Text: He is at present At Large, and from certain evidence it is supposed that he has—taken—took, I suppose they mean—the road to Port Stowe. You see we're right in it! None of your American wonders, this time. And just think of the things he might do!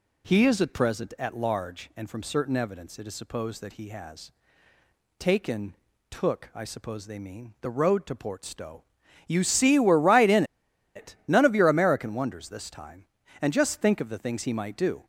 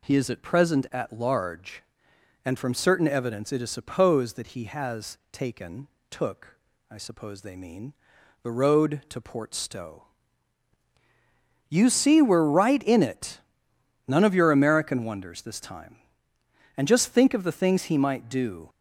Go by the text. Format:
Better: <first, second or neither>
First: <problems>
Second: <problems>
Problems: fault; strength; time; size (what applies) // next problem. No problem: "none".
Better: second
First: pauses between "in" and "it"; noticeable; at 10.4 s; 0.51 s long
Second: none